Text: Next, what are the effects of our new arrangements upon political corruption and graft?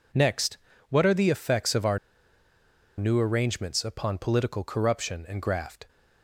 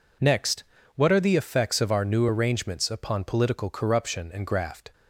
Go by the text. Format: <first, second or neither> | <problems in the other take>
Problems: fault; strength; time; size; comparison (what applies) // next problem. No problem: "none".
second | pauses between "our" and "new"; at 1.9 s; 0.99 s long